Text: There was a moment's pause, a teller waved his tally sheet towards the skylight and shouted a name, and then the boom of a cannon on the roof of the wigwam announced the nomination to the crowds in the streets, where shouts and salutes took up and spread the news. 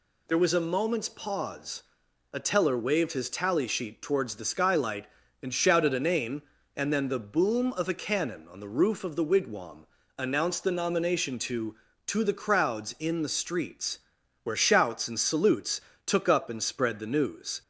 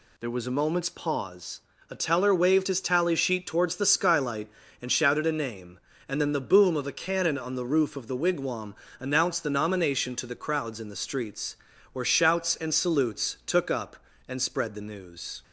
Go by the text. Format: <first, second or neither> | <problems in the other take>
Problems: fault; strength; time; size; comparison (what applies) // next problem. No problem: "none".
second | pauses between "wigwam" and "announced"; slight; at 9.8 s; 0.32 s long; slight in the second // says "to" twice; at 12.0 s // pauses between "salutes" and "took"; slight; at 15.7 s; 0.26 s long